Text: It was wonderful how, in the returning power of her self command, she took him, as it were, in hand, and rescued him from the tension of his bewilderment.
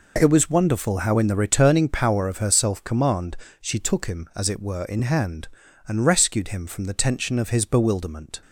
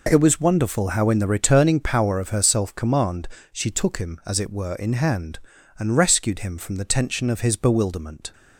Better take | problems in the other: neither | none

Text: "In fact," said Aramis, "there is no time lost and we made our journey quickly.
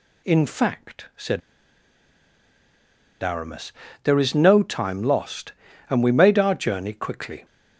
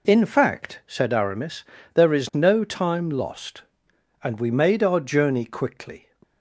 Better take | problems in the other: second | pauses between "said" and "Aramis"; strong; at 1.4 s; 1.8 s long

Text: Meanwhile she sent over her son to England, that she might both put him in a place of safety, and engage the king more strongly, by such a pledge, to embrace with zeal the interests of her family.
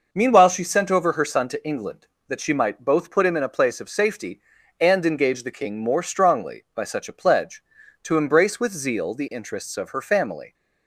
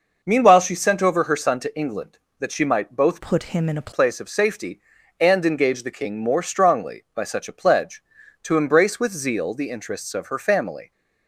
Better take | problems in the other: first | changes voice from "put" to "a"; from 3.1 to 3.9 s; 0.8 s long

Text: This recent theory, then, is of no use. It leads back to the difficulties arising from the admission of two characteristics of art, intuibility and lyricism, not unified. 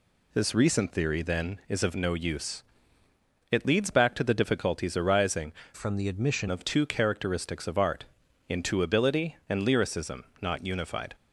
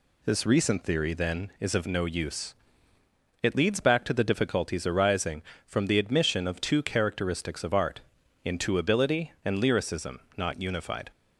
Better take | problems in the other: second | changes voice from "from" to "admission"; from 5.7 to 6.4 s; 0.7 s long

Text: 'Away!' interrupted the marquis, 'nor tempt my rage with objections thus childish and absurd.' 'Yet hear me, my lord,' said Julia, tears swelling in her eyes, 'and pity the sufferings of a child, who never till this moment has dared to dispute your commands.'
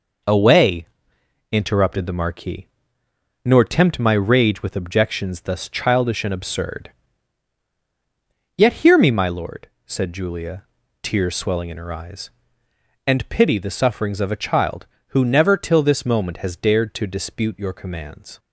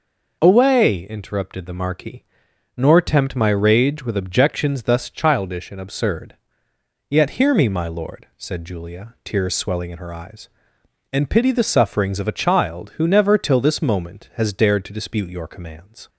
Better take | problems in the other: neither | none

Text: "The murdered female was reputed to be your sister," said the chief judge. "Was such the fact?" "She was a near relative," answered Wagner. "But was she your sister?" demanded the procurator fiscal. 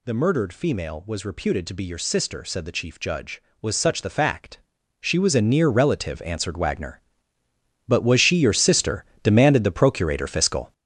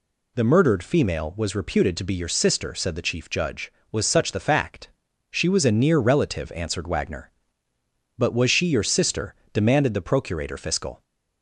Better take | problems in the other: second | gets louder; strong; throughout; 7.5 dB

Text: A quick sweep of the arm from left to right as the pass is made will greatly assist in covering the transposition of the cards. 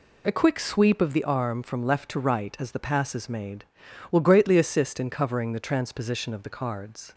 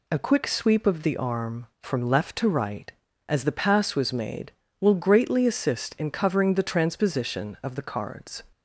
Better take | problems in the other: first | says "was" for "is"; at 3.9 s

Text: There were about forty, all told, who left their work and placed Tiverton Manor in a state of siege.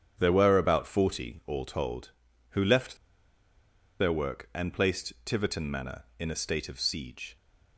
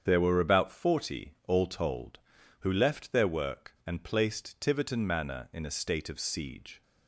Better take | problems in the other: second | starts louder than the rest; strong; until 1.2 s; 8 dB; strong in the second // pauses between "left" and "their"; at 2.9 s; 1.0 s long

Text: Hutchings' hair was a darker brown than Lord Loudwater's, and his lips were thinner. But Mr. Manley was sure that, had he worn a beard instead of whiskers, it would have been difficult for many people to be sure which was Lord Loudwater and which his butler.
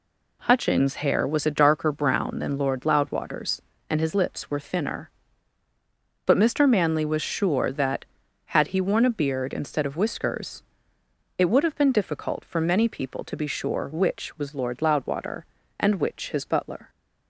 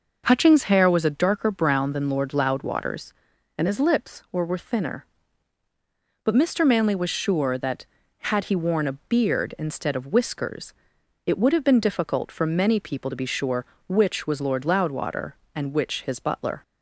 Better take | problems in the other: first | says "were" twice; at 4.4 s

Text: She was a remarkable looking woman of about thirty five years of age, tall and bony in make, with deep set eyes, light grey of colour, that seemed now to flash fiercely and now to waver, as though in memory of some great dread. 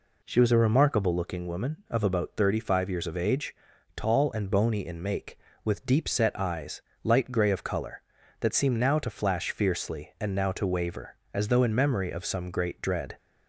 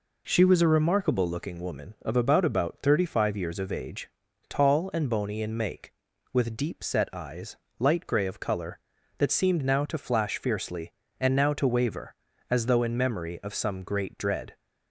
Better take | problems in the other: first | says "about" twice; at 2.4 s

